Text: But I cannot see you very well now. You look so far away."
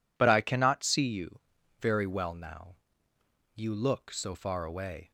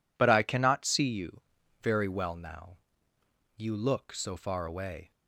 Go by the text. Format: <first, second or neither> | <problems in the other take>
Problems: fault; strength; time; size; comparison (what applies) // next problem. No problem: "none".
neither | pauses between "you" and "very"; the same in both